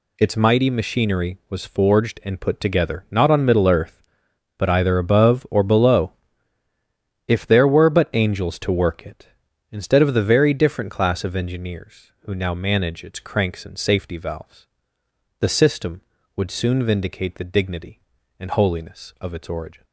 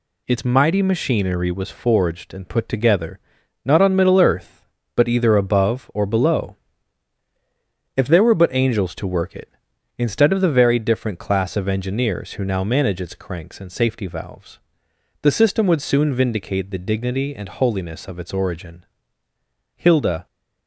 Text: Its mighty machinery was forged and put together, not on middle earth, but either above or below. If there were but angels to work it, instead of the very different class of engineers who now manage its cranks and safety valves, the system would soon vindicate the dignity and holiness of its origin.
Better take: first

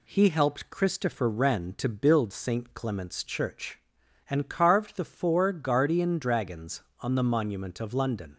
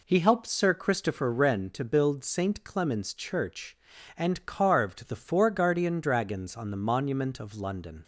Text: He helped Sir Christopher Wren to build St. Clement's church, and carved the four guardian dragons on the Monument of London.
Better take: second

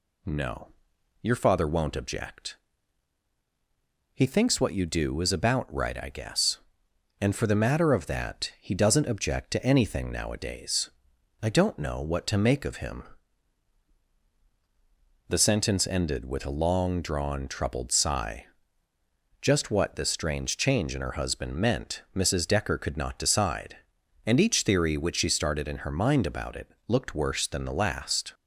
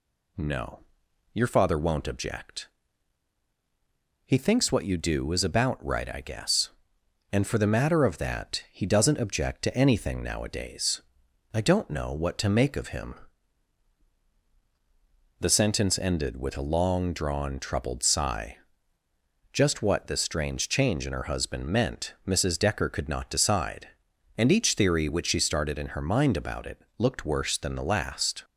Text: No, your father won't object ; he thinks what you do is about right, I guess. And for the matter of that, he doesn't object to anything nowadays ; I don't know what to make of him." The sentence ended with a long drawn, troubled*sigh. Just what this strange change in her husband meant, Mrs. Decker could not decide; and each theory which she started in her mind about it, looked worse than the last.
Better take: neither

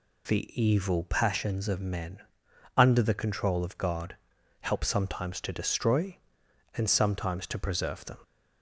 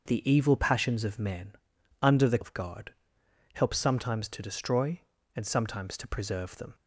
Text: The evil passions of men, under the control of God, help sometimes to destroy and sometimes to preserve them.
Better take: first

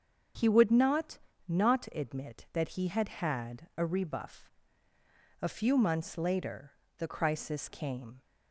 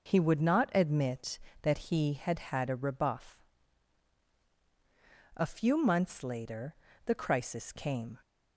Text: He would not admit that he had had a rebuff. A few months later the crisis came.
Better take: second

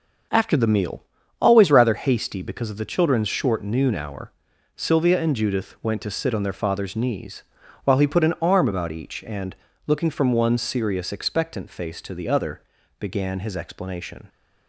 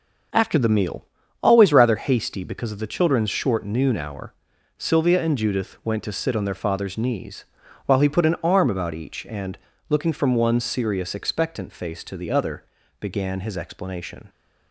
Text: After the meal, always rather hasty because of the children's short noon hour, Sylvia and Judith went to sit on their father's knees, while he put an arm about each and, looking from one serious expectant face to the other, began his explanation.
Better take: neither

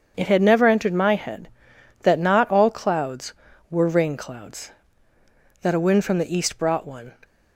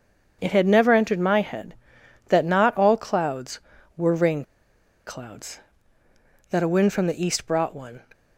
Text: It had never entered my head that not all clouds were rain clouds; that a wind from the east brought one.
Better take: first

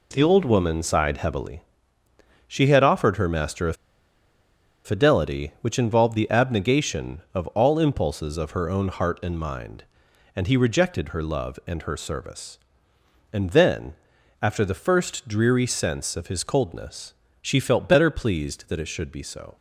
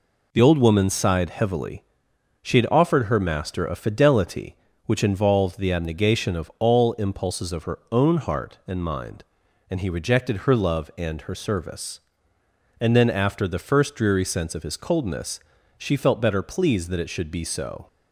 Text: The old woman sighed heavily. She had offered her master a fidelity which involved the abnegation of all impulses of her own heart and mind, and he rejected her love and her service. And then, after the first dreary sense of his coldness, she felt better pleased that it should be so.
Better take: second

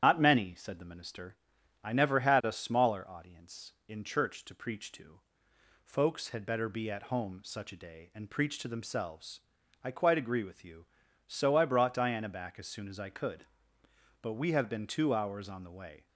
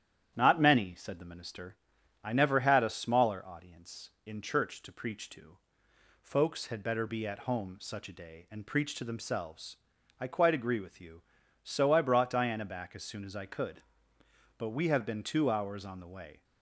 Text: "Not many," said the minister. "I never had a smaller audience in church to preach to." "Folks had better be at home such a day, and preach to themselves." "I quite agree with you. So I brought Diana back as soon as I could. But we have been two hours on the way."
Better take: second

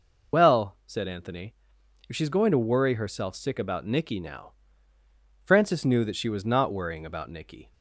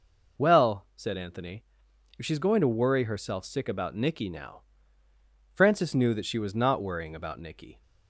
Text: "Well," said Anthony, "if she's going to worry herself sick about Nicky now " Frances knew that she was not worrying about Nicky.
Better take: second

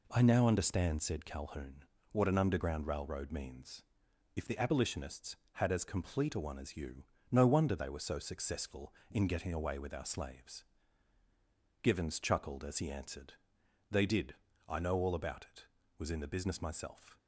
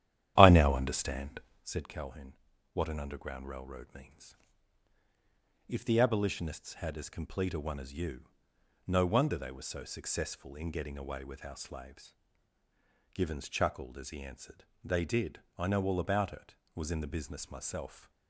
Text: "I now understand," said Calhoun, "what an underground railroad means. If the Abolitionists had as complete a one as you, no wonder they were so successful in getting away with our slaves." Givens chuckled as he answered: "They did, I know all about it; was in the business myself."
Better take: first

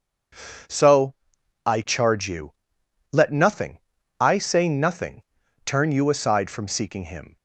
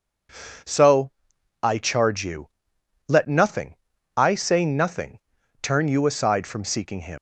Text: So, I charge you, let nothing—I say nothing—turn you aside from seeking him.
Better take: first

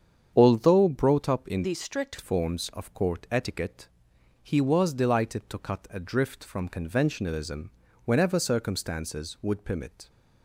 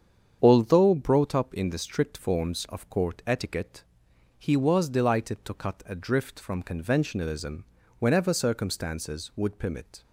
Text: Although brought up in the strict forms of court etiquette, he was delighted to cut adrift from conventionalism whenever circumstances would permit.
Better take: second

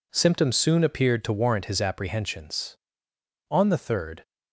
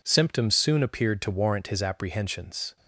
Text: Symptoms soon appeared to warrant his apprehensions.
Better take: second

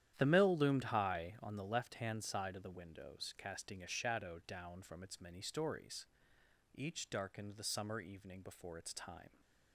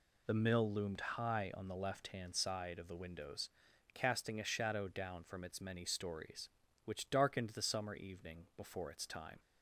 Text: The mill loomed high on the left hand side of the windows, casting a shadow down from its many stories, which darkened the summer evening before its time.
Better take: second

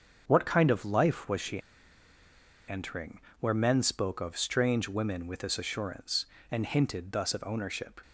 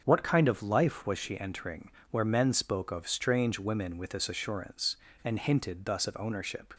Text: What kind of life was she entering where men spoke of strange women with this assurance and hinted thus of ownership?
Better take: second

